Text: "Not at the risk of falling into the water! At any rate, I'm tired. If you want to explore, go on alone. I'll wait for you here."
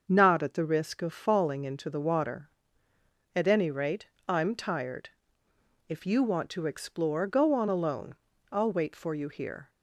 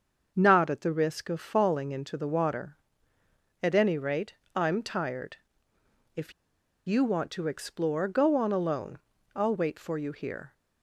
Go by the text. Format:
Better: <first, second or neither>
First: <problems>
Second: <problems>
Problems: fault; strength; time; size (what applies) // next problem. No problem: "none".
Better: first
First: starts louder than the rest; until 1.0 s; 6.5 dB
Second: starts louder than the rest; until 1.3 s; 6.5 dB // pauses between "If" and "you"; noticeable; at 6.3 s; 0.54 s long